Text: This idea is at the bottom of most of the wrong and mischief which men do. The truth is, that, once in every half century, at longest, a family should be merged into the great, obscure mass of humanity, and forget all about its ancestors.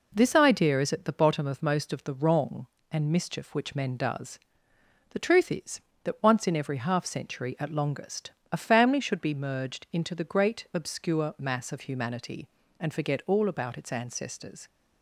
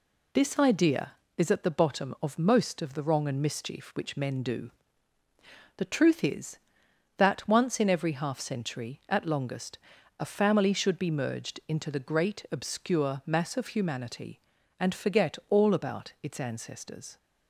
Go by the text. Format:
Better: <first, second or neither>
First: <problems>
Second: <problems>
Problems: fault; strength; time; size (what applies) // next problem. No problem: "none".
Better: second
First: says "does" for "do"; at 3.9 s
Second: none